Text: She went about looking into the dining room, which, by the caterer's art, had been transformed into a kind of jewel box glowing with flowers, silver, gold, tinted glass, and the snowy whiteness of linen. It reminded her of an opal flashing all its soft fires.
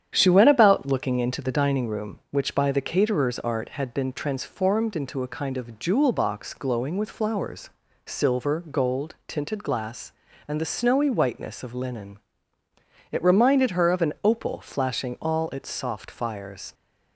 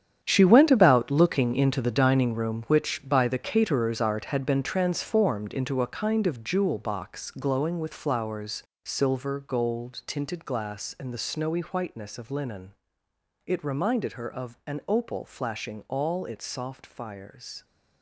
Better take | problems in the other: first | gets quieter; strong; throughout; 12 dB // starts louder than the rest; strong; until 1.2 s; 9 dB; strong in the first

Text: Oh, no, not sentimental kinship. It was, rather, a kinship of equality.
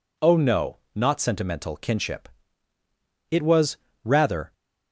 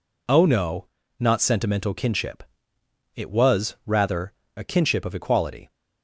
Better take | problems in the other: second | stops before "a kinship of equality"; at 4.5 s

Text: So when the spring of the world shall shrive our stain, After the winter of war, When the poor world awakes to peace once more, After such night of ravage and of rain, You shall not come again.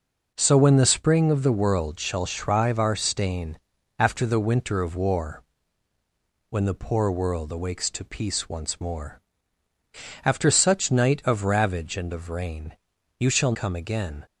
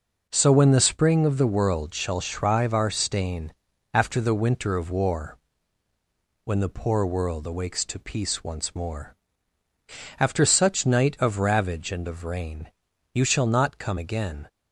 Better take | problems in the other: second | skips "not"; at 13.5 s

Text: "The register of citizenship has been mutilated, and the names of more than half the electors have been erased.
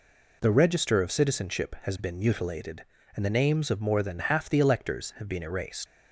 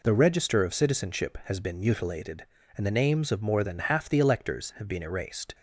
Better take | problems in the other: second | leaves "erased" unfinished; at 5.8 s; 90 ms

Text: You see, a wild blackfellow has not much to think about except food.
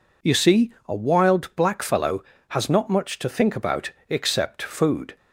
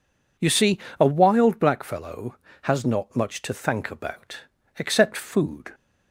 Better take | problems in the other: first | says "thank" for "think"; at 3.5 s // pauses between "about" and "except"; at 4.3 s; 0.40 s long; slight in the first

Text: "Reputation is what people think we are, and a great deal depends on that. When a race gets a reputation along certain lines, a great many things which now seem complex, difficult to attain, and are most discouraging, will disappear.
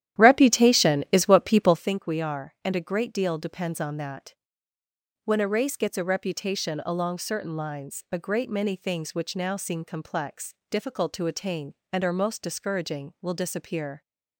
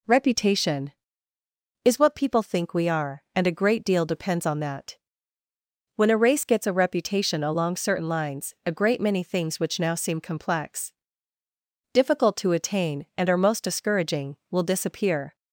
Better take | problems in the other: second | starts louder than the rest; strong; until 2.0 s; 11.5 dB

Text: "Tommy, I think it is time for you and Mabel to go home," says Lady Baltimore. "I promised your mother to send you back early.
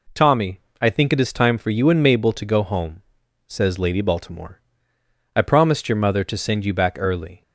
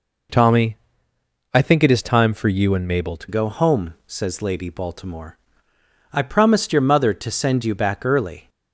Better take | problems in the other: first | changes voice at "go"; from 3.2 s on; 5.2 s long

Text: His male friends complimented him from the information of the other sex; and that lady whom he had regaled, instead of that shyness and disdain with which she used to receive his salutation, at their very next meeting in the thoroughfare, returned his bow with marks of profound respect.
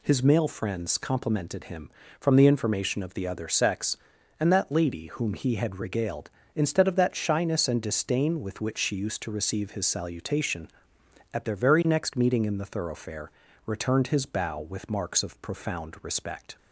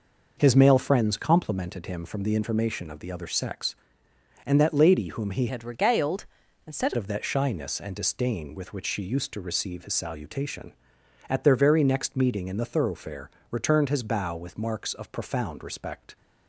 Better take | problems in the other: first | changes voice from "had" to "instead"; from 5.4 to 6.9 s; 1.5 s long

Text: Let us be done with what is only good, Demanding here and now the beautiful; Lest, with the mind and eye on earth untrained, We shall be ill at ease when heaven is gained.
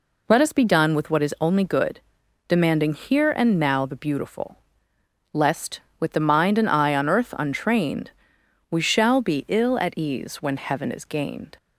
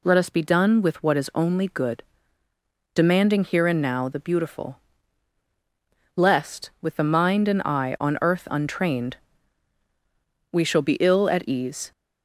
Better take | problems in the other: first | stops before "when heaven is gained"; at 11.9 s

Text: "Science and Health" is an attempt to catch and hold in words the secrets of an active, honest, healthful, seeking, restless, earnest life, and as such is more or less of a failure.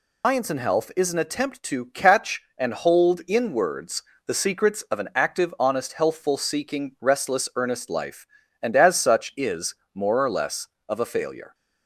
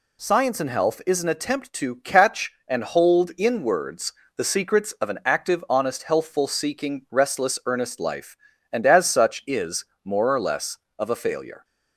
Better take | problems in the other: second | loses the start of "Science"; at 0.2 s; 150 ms // pauses between "words" and "the"; slight; at 4.0 s; 0.24 s long; slight in the second // pauses between "is" and "more"; slight; at 9.7 s; 0.18 s long; slight in the second

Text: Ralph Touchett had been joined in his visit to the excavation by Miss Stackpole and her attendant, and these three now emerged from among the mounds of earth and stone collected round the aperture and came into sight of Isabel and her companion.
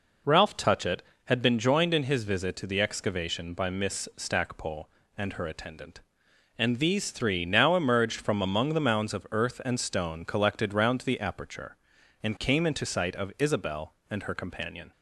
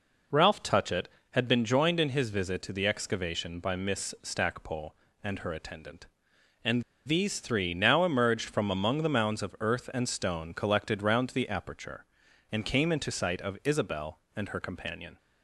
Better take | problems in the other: first | pauses between "and" and "these"; slight; at 6.8 s; 0.23 s long

